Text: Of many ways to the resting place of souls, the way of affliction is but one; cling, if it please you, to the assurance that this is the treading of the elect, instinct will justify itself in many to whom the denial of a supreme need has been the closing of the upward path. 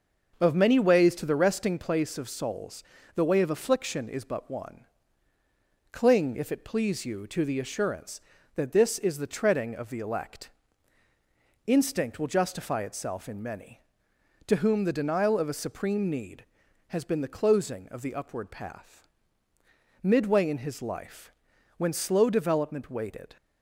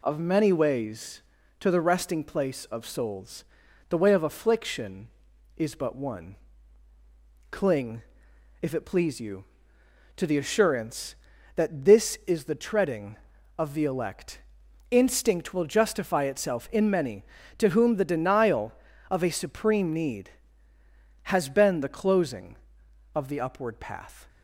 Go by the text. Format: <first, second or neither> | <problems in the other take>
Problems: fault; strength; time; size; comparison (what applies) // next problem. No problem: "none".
second | starts louder than the rest; until 1.4 s; 6.5 dB // goes on to say "Midway in his life when slow development waited"; strong; from 20.0 s on; 3.3 s long